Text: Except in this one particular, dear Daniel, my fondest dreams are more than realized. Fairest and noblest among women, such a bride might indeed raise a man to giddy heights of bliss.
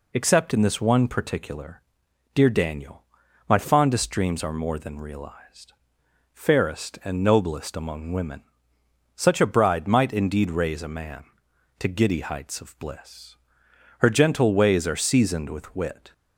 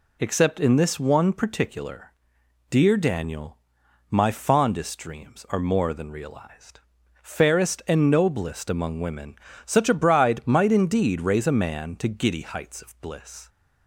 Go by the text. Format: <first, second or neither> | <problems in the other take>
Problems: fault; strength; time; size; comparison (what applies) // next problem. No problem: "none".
second | goes on to say "Her gentle ways are seasoned with wit"; strong; from 13.9 s on; 2.1 s long